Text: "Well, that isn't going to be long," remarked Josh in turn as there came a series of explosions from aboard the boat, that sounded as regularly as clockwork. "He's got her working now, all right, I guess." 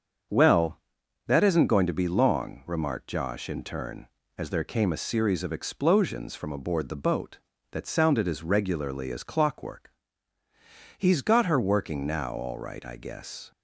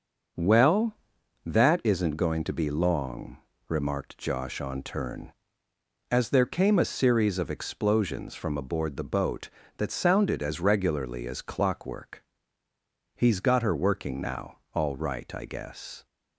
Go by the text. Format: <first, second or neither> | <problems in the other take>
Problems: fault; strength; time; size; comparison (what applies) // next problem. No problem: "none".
first | starts louder than the rest; noticeable; until 1.8 s; 6 dB; also in the first // says "on" for "in"; at 4.5 s